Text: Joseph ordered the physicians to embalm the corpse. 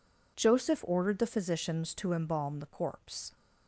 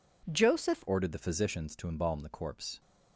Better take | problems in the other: first | changes voice at "ordered"; from 0.8 s on; 2.0 s long

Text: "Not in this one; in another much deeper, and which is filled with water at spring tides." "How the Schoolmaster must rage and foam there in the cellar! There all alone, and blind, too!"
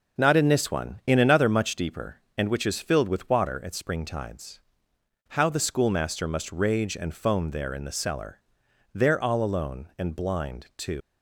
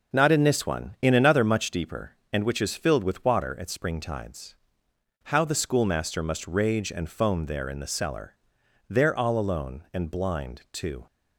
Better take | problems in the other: second | leaves "too" unfinished; at 11.0 s; 105 ms

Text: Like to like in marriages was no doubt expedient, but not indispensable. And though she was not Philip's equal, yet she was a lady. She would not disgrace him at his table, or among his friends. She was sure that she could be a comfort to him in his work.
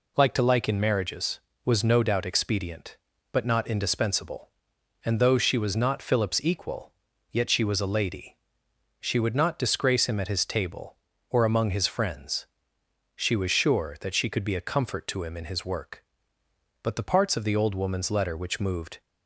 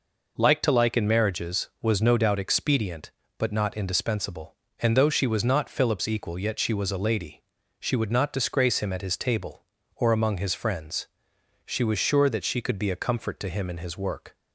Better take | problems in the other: second | goes on to say "But the parts of the old woman's letter which moved"; strong; from 16.8 s on; 2.1 s long

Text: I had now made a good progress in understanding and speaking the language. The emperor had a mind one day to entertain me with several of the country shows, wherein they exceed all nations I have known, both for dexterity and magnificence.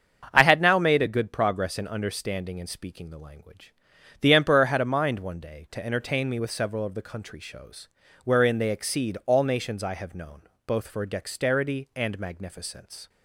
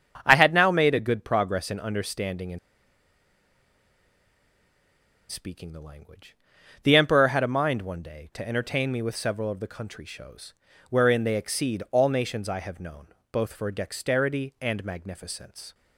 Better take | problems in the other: first | starts louder than the rest; strong; until 1.2 s; 7.5 dB; strong in the first // pauses between "and" and "speaking"; strong; at 2.5 s; 2.7 s long

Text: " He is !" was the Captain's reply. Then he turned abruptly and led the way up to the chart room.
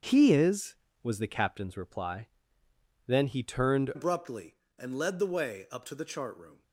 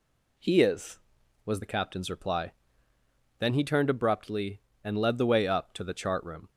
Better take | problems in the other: second | starts louder than the rest; until 1.1 s; 6.5 dB // changes voice at "abruptly"; from 3.9 s on; 2.7 s long

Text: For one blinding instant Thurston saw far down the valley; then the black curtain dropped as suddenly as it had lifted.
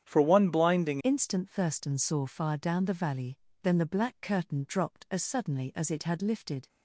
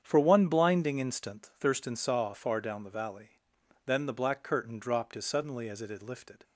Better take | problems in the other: second | starts louder than the rest; strong; until 1.0 s; 9 dB; strong in the second // changes voice at "instant"; from 1.0 s on; 5.6 s long

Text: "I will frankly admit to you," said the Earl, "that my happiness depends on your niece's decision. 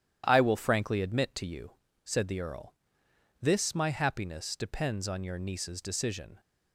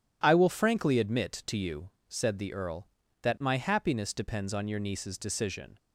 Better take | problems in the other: second | starts louder than the rest; strong; until 1.2 s; 11 dB // says "this" for "that"; at 3.4 s

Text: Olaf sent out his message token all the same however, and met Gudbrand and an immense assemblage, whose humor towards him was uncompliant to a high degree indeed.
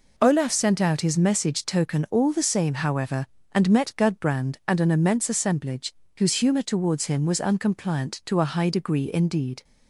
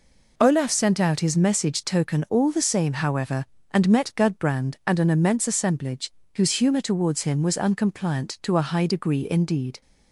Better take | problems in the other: neither | none

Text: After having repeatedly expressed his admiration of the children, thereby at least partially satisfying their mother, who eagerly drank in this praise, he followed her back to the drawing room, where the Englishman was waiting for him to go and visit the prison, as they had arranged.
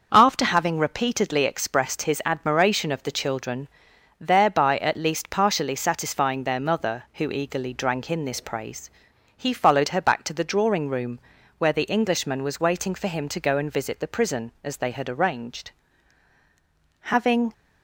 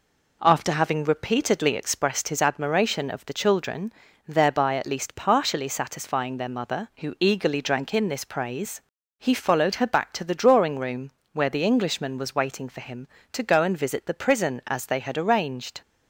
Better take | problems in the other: second | starts louder than the rest; until 1.1 s; 6 dB // goes on to say "Having"; from 17.0 s on; 0.52 s long

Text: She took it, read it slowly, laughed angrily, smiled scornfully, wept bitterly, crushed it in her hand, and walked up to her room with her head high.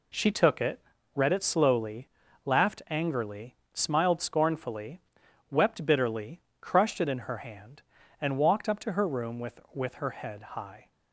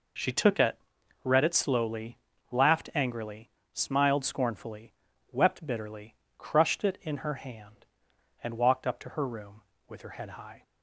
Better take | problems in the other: second | says "with" twice; at 9.7 s

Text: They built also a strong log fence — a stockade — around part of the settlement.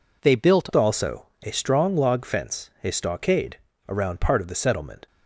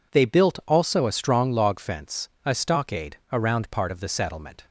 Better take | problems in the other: second | changes voice at "also"; from 0.7 s on; 4.3 s long // pauses between "also" and "a"; slight; at 1.2 s; 0.16 s long

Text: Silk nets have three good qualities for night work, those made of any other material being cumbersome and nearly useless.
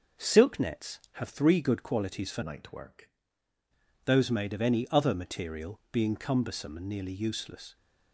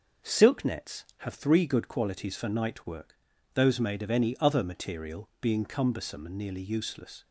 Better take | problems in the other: second | changes voice from "night" to "work"; from 2.4 to 3.1 s; 0.7 s long

